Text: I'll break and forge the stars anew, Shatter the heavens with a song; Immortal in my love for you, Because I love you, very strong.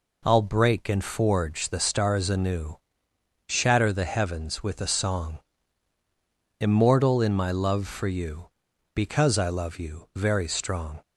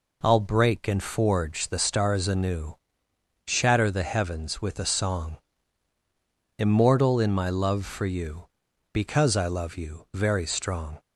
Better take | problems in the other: neither | none

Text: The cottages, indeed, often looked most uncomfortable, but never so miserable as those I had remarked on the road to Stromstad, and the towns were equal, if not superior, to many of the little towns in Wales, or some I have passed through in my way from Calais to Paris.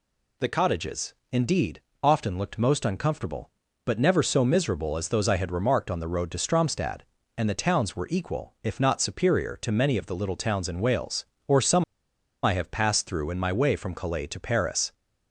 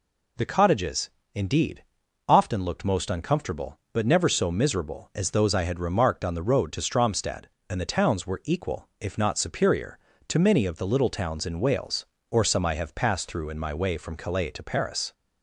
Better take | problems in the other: second | pauses between "some" and "I"; noticeable; at 11.8 s; 0.61 s long

